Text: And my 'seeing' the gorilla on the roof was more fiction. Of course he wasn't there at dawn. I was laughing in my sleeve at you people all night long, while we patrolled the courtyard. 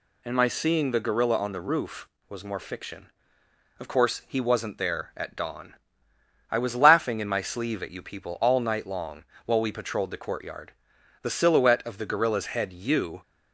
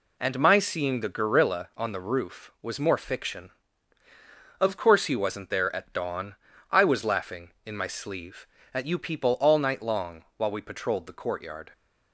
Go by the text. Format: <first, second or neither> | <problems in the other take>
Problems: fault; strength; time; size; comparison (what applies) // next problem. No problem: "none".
second | goes on to say "The silhouette of the gorilla's head you"; strong; from 11.2 s on; 2.0 s long